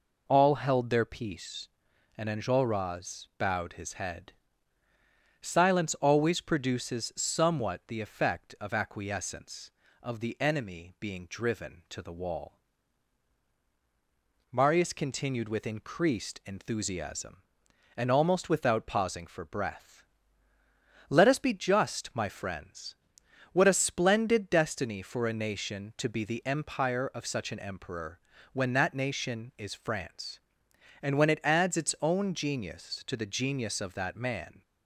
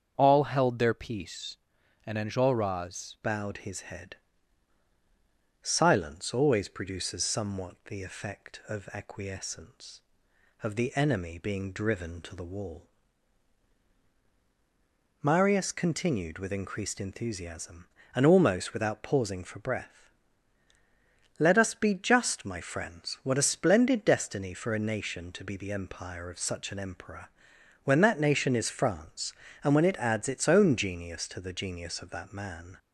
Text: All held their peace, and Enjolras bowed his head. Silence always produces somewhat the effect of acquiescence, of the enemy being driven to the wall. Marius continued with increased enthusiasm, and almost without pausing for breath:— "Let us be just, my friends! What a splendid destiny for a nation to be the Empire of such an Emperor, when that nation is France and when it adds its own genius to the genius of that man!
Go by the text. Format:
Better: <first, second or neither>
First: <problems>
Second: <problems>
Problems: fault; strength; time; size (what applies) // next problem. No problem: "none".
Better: first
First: none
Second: starts louder than the rest; until 1.1 s; 7 dB // changes voice at "bowed"; from 3.2 s on; 29.5 s long